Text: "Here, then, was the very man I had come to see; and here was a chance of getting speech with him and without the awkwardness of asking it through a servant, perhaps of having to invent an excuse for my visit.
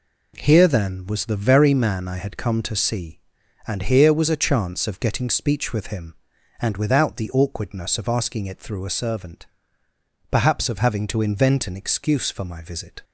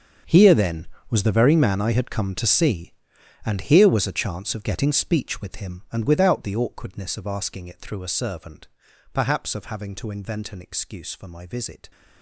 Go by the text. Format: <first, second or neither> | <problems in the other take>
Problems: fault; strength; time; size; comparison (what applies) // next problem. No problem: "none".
first | gets quieter; strong; throughout; 15.5 dB